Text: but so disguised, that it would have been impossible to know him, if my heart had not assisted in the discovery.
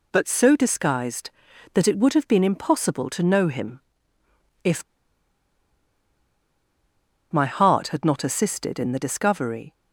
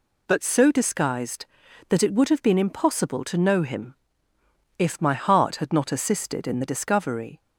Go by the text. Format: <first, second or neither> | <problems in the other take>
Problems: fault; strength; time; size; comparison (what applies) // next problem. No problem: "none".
second | pauses between "if" and "my"; strong; at 4.8 s; 2.4 s long